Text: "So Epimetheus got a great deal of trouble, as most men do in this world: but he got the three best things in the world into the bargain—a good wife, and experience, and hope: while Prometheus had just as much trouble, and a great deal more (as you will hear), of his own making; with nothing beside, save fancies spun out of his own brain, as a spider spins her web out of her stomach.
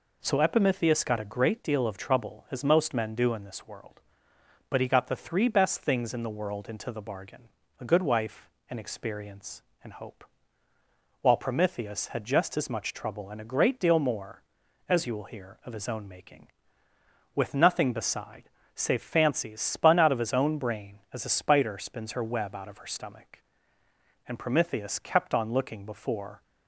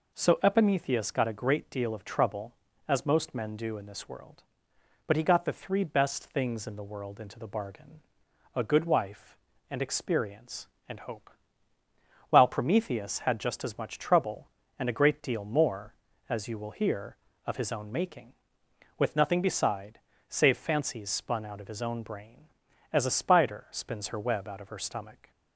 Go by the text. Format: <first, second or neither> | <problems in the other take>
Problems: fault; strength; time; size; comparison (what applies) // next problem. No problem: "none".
second | goes on to say "And Prometheus kept on looking before"; strong; from 24.2 s on; 2.1 s long